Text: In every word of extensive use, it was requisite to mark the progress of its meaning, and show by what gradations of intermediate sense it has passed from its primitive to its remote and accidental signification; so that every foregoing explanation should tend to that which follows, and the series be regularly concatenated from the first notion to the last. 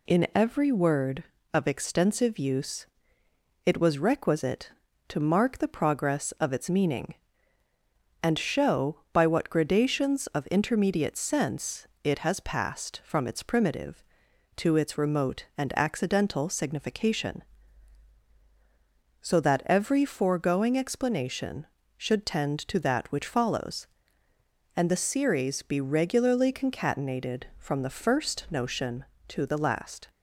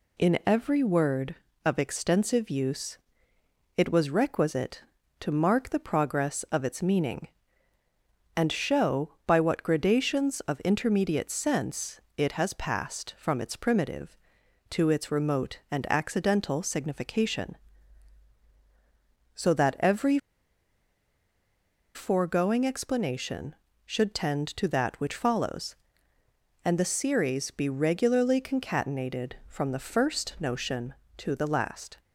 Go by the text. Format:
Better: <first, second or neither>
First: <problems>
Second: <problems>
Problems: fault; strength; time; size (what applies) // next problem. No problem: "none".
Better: first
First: pauses between "sense" and "it"; slight; at 11.8 s; 0.16 s long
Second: pauses between "sense" and "it"; slight; at 12.0 s; 0.16 s long // pauses between "every" and "foregoing"; strong; at 20.1 s; 1.7 s long